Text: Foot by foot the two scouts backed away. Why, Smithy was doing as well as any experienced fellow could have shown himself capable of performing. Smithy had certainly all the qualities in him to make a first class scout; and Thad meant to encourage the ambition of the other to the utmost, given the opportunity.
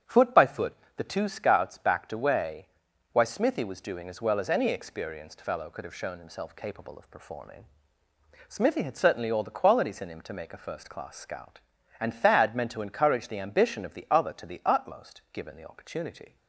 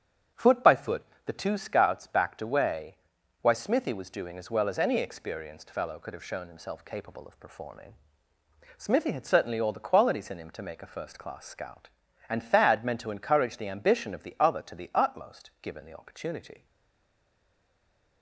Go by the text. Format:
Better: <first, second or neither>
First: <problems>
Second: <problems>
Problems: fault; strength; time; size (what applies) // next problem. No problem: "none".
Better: first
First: starts louder than the rest; strong; until 1.2 s; 8.5 dB // pauses between "foot" and "the"; slight; at 0.7 s; 0.20 s long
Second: starts louder than the rest; strong; until 1.5 s; 8.5 dB // pauses between "foot" and "the"; slight; at 1.0 s; 0.20 s long // stays silent after the last word; noticeable; from 16.6 s on; 1.6 s long